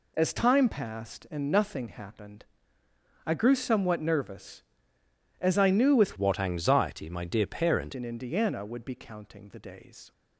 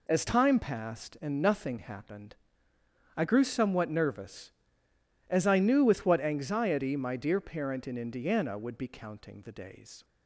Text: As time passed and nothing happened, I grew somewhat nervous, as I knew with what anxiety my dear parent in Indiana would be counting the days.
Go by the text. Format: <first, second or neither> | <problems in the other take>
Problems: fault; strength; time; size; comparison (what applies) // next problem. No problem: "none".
second | changes voice from "what" to "parent"; from 6.1 to 7.9 s; 1.8 s long